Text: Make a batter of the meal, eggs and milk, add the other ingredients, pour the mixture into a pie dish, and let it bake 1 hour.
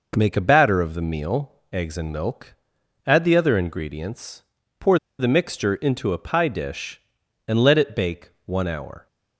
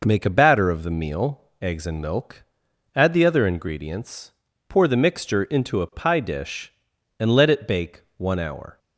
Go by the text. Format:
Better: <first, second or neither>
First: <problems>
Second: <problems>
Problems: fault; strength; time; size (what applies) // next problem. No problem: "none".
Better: second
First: pauses between "pour" and "the"; slight; at 4.9 s; 0.22 s long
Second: none